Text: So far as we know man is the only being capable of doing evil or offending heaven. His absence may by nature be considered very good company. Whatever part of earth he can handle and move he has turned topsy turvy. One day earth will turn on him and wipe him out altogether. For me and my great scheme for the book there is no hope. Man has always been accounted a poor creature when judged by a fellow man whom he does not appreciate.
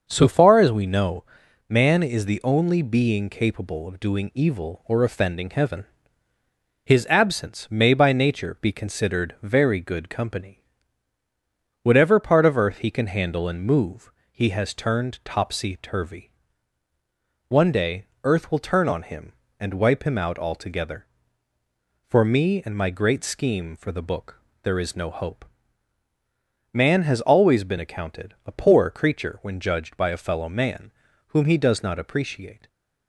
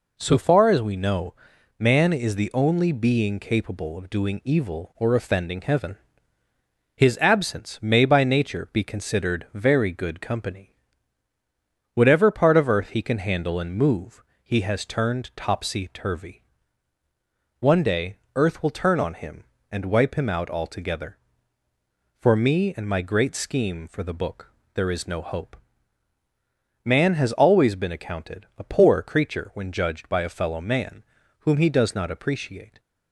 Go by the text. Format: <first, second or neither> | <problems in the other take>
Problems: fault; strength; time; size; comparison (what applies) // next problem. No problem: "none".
second | starts louder than the rest; until 1.1 s; 6 dB // pauses between "know" and "man"; at 1.2 s; 0.44 s long; also in the second // pauses between "move" and "he"; slight; at 14.0 s; 0.22 s long; slight in the second // pauses between "day" and "earth"; slight; at 18.0 s; 0.18 s long; slight in the second // pauses between "book" and "there"; slight; at 24.3 s; 0.22 s long; slight in the second // pauses between "man" and "whom"; at 30.9 s; 0.40 s long; also in the second